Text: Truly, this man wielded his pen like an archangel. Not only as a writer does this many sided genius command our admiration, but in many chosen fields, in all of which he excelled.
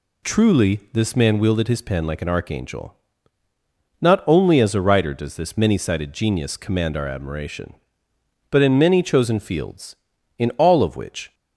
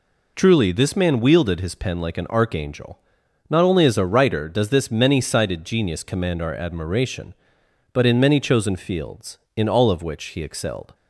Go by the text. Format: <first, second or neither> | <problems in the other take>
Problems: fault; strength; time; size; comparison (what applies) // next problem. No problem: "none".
second | stops before "he excelled"; at 11.3 s